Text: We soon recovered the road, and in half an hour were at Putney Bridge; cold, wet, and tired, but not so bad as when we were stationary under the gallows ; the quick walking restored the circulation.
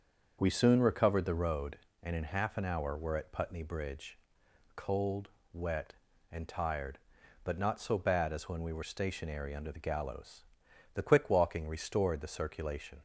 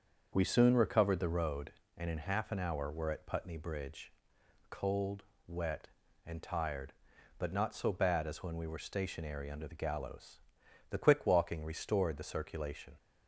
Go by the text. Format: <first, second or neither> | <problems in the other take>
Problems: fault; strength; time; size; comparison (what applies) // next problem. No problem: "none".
neither | starts louder than the rest; the same in both